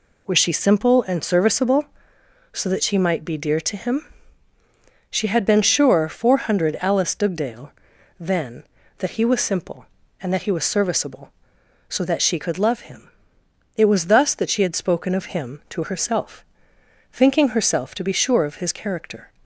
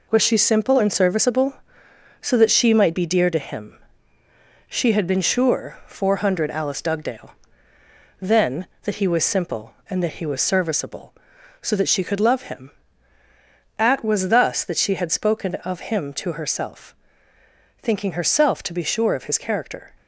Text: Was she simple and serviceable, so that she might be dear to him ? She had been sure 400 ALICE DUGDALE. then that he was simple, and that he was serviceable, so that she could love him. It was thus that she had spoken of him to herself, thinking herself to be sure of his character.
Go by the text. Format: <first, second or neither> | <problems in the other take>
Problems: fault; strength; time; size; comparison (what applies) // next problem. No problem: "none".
first | says "At" for "It"; at 13.7 s